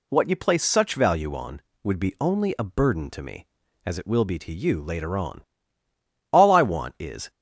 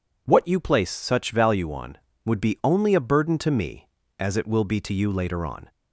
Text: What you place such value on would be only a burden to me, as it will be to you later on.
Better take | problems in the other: second | goes on to say "All I want is"; noticeable; from 6.3 s on; 0.98 s long

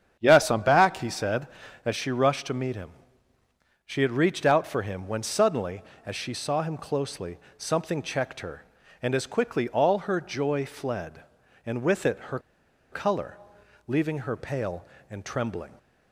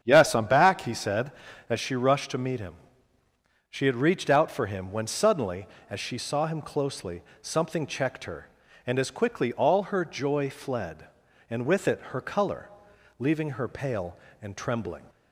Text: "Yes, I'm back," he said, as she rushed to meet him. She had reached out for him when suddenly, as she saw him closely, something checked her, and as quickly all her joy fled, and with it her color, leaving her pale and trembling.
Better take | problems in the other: second | starts louder than the rest; strong; until 1.2 s; 8.5 dB; strong in the second // pauses between "her" and "color"; noticeable; at 12.3 s; 0.52 s long

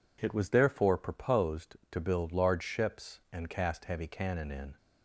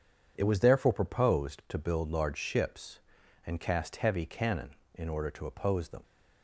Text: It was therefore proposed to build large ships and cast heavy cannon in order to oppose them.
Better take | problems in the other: second | stops before "order to oppose them"; at 4.7 s

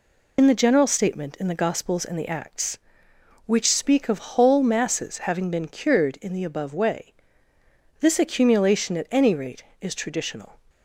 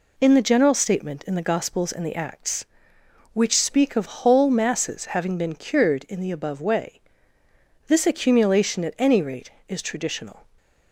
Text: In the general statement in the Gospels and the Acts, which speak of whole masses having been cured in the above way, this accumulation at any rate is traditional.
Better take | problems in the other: second | loses the start of "In"; at 0.3 s; 75 ms

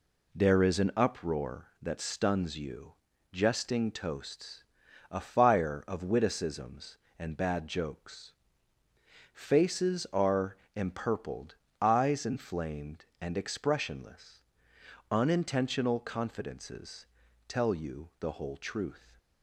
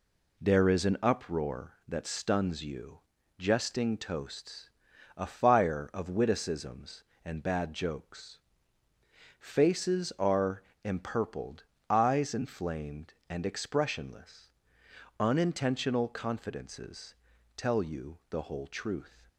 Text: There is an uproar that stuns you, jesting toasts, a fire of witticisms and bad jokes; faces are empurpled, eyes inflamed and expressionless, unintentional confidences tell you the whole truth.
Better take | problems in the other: neither | pauses between "are" and "empurpled"; slight; the same in both // pauses between "confidences" and "tell"; the same in both

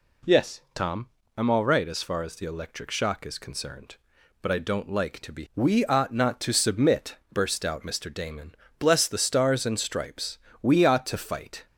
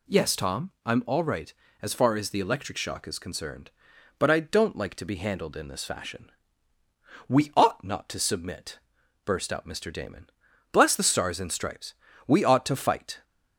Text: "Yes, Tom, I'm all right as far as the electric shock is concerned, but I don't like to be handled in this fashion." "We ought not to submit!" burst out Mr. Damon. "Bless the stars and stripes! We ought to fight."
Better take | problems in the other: second | skips "handled in this fashion"; at 5.4 s

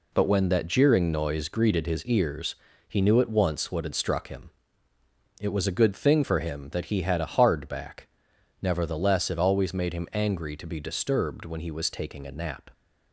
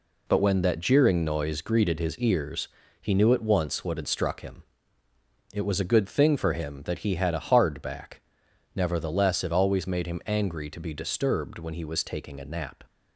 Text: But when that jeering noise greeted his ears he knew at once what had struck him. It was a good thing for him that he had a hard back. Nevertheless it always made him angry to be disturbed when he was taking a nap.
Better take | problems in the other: neither | pauses between "ears" and "he"; slight; the same in both

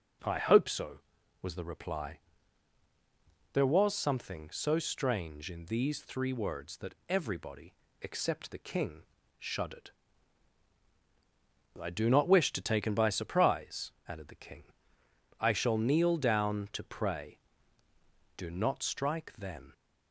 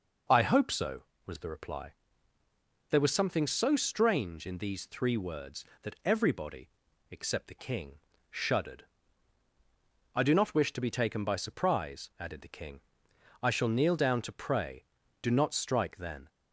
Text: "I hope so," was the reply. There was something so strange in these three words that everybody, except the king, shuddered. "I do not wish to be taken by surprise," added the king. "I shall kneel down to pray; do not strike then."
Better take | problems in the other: second | skips "be"; at 12.6 s

